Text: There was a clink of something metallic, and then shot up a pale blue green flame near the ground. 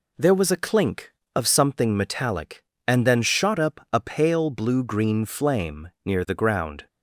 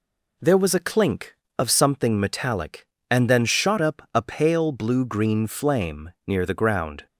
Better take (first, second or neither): neither